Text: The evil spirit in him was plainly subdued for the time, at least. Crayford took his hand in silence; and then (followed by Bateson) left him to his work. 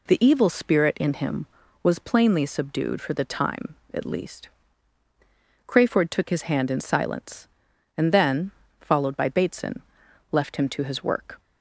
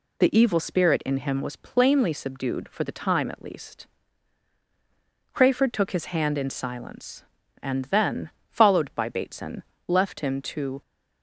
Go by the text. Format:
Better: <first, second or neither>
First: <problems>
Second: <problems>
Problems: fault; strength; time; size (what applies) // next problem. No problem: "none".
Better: first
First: none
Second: stops before "his work"; at 10.8 s